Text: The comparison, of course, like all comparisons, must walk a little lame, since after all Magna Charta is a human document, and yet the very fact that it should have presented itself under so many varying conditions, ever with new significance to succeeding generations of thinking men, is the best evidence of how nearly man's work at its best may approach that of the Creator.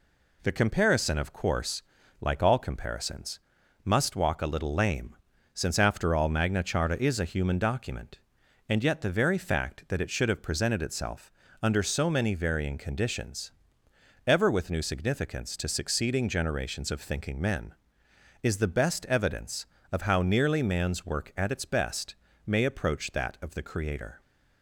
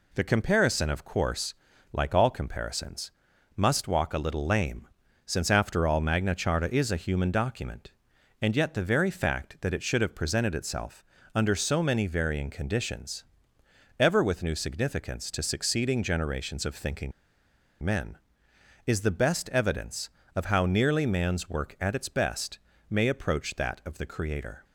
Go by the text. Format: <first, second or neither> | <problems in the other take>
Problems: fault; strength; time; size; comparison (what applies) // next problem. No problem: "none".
first | pauses between "itself" and "under"; slight; at 11.0 s; 0.32 s long; slight in the first // pauses between "thinking" and "men"; noticeable; at 17.1 s; 0.72 s long // pauses between "best" and "may"; slight; at 22.5 s; 0.32 s long; slight in the first